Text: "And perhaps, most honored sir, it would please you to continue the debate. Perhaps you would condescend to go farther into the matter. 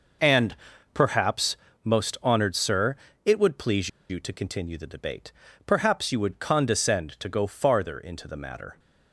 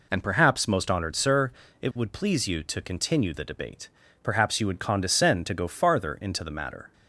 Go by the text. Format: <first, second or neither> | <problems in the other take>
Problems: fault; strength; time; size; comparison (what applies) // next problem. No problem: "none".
second | pauses between "And" and "perhaps"; at 0.5 s; 0.38 s long // pauses between "please" and "you"; slight; at 3.8 s; 0.20 s long